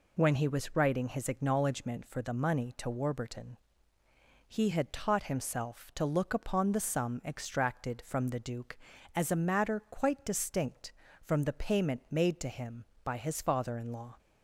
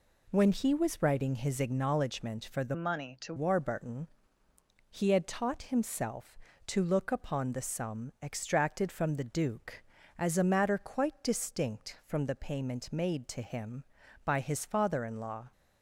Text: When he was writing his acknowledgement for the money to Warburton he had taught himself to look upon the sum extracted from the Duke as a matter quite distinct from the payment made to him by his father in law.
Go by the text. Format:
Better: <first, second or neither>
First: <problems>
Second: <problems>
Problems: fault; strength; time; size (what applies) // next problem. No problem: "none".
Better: first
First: pauses between "Warburton" and "he"; noticeable; at 3.5 s; 0.90 s long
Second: changes voice from "money" to "to"; from 2.7 to 3.3 s; 0.6 s long // pauses between "Warburton" and "he"; noticeable; at 4.0 s; 0.82 s long